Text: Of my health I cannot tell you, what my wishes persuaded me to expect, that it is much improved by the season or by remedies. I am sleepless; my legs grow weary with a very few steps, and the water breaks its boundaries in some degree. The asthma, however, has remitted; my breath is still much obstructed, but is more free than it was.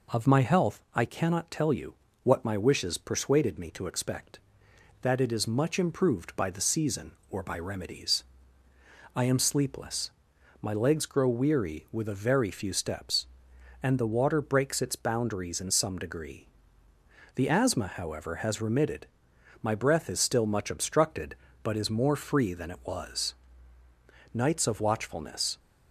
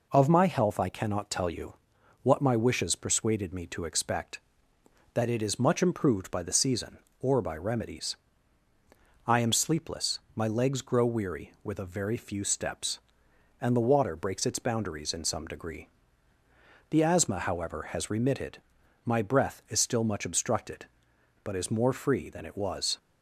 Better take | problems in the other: second | goes on to say "Nights of watchfulness"; noticeable; from 24.3 s on; 1.2 s long

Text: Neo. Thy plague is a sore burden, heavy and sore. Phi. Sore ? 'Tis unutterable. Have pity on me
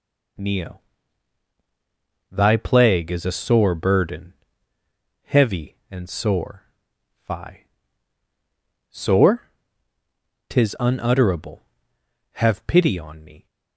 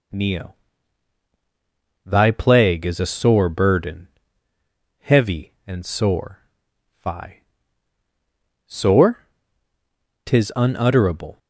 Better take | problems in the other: first | stops before "Have pity on me"; at 11.3 s

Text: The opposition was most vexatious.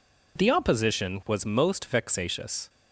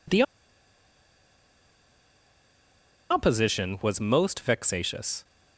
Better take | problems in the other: first | pauses between "The" and "opposition"; strong; at 0.2 s; 2.8 s long

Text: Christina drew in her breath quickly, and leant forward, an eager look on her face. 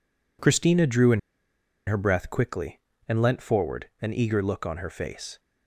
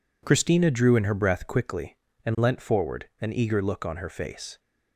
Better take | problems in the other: second | pauses between "in" and "her"; noticeable; at 1.1 s; 0.67 s long

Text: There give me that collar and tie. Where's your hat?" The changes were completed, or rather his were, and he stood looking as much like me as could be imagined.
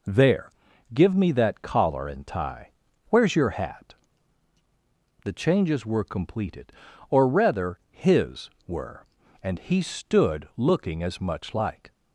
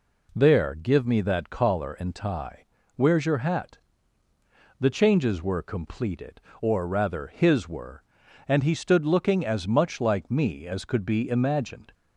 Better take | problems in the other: second | pauses between "There" and "give"; at 0.5 s; 0.42 s long // stops before "me as could be imagined"; at 11.9 s

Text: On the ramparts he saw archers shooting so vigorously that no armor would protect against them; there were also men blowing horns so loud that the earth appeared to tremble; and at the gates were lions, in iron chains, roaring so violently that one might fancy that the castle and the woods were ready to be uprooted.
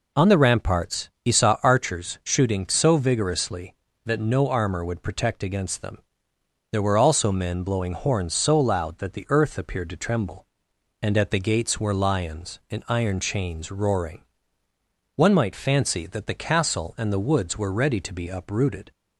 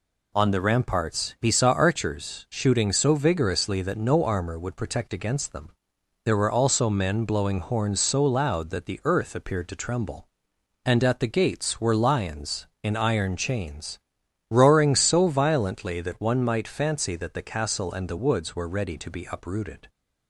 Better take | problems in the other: second | skips "so violently that"; at 14.6 s

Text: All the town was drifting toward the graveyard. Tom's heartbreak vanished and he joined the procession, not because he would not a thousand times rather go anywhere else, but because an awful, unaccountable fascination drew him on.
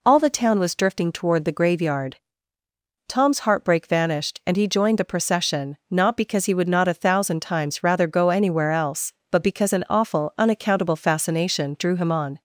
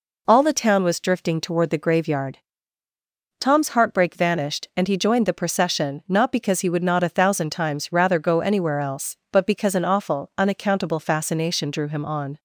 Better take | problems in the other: neither | none

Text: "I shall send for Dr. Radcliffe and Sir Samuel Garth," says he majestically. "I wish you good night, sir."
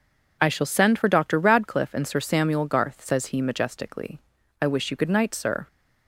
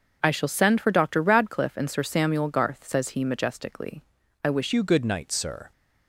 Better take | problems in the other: first | starts louder than the rest; until 1.2 s; 6.5 dB // changes voice at "you"; from 4.7 s on; 1.0 s long

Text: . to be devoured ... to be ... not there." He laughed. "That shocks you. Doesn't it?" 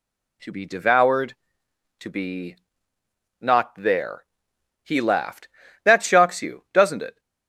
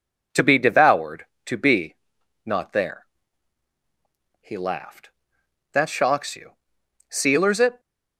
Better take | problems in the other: first | says "Sealers" for "Doesn't"; at 7.0 s

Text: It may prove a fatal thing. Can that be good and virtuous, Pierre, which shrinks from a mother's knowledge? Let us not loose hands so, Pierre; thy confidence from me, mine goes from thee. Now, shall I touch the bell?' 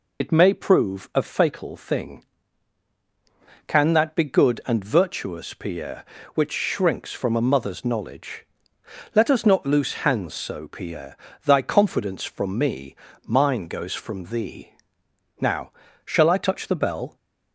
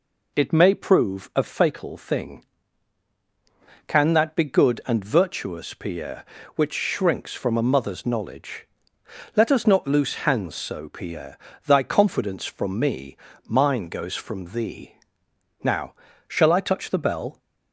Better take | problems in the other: second | loses the start of "It"; at 0.2 s; 65 ms

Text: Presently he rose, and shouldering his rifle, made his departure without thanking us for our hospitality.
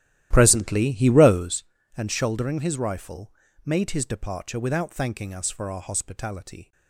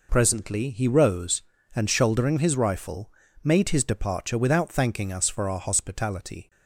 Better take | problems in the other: second | starts louder than the rest; strong; until 1.5 s; 13 dB

